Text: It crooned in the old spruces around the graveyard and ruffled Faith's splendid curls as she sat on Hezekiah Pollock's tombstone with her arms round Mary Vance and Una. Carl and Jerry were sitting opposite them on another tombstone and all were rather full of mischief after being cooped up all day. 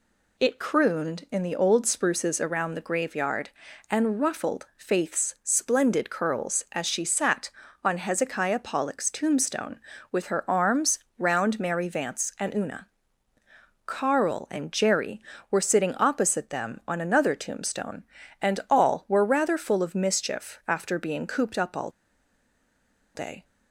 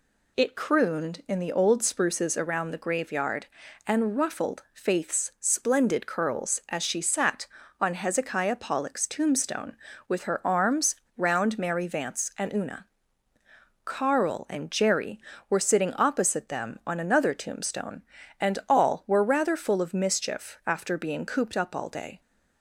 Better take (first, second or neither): second